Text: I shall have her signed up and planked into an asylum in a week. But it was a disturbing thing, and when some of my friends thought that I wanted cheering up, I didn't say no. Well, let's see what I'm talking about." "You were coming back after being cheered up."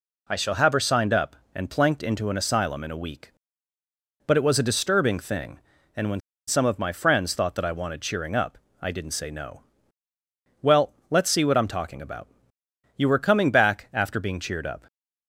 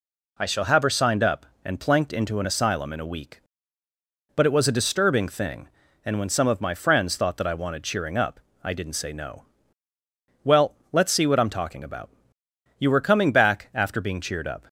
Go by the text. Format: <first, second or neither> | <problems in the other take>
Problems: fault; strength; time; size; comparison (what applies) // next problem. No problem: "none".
second | pauses between "when" and "some"; slight; at 6.2 s; 0.27 s long